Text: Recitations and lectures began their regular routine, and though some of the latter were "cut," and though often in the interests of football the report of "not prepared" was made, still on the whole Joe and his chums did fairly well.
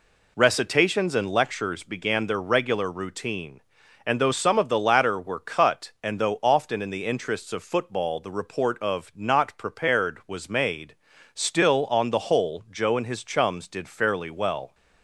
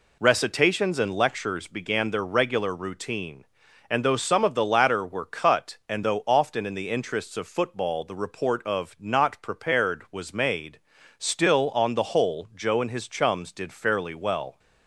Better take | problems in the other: neither | none

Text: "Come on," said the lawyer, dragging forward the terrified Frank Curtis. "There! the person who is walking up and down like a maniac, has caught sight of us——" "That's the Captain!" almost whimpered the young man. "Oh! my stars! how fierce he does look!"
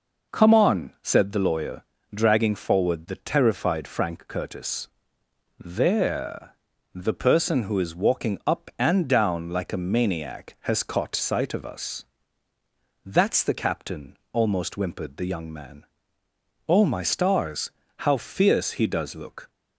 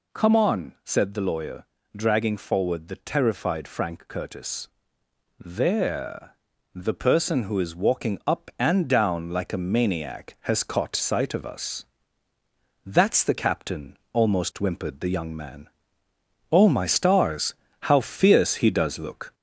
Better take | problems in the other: first | gets louder; slight; throughout; 2.5 dB

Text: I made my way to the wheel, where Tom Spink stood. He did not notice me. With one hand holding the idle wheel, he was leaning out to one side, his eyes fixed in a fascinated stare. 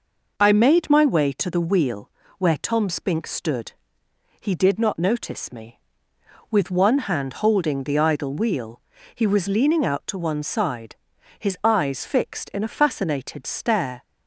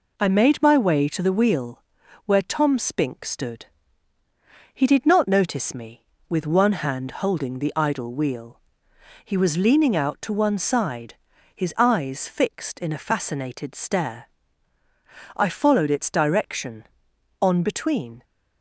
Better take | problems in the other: first | goes on to say "I followed its direction on between"; strong; from 15.3 s on; 2.8 s long

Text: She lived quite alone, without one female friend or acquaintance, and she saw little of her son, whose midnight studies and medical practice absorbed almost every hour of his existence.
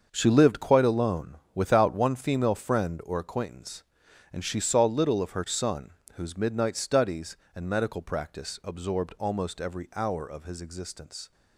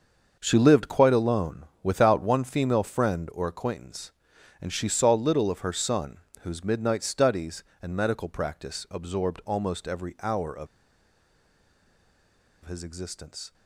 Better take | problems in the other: first | starts louder than the rest; until 1.4 s; 6.5 dB; also in the first // pauses between "of" and "his"; strong; at 10.6 s; 1.9 s long

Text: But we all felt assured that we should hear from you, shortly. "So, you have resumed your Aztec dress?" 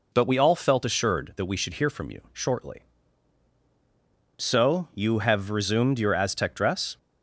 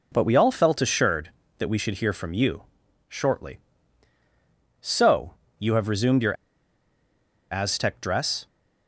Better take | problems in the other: first | pauses between "your" and "Aztec"; at 6.3 s; 1.1 s long

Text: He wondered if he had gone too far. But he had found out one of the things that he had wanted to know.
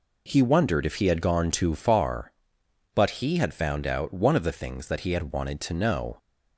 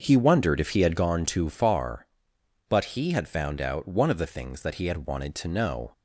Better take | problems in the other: first | starts louder than the rest; until 1.1 s; 6.5 dB

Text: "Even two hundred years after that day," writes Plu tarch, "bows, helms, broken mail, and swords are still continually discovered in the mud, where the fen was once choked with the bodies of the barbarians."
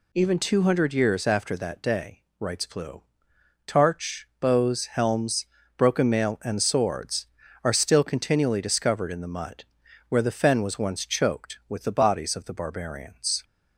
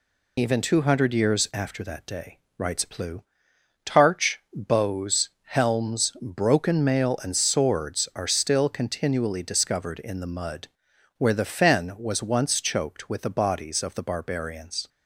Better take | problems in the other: first | loses the start of "Even"; at 0.3 s; 50 ms // pauses between "Plu" and "tarch"; noticeable; at 3.2 s; 0.62 s long; noticeable in the first

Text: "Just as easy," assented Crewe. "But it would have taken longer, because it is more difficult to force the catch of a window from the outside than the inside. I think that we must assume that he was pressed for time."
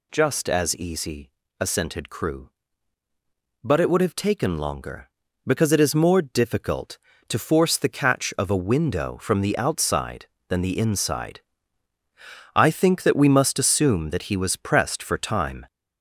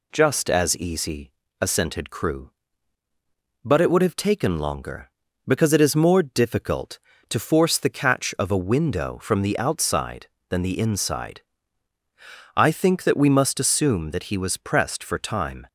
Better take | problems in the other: second | gets louder; noticeable; throughout; 4.5 dB

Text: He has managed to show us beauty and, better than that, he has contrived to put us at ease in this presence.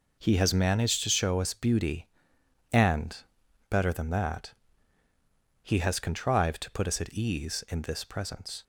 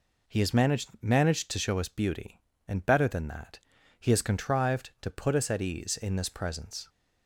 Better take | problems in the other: first | says "managed" twice; at 1.0 s

